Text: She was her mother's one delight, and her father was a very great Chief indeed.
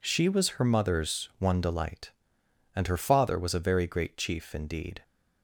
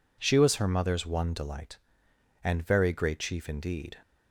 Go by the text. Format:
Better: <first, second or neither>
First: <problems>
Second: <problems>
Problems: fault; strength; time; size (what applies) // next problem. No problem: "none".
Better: first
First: none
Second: skips "her father was a"; at 2.6 s